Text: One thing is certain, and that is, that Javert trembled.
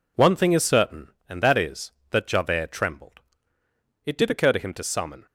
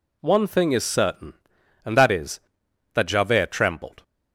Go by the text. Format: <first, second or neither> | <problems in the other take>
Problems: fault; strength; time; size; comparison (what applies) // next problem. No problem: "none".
second | goes on to say "It did occur to him to summon"; noticeable; from 4.0 s on; 1.2 s long